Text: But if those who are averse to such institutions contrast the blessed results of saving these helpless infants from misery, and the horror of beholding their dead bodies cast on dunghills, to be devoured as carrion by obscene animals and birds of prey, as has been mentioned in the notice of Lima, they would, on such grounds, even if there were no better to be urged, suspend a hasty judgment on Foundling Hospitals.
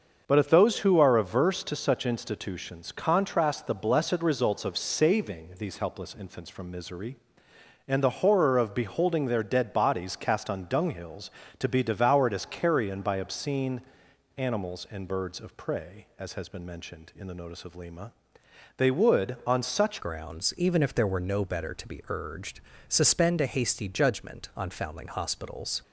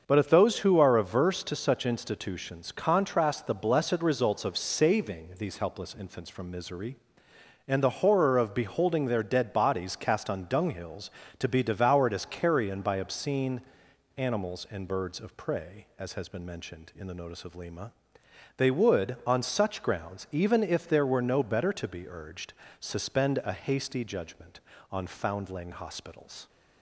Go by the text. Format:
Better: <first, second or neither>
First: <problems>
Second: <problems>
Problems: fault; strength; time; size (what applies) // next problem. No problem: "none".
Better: second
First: starts louder than the rest; until 1.2 s; 6.5 dB // pauses between "obscene" and "animals"; noticeable; at 13.8 s; 0.58 s long // changes voice at "grounds"; from 20.0 s on; 5.8 s long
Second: starts louder than the rest; until 1.0 s; 6.5 dB // pauses between "obscene" and "animals"; noticeable; at 13.6 s; 0.58 s long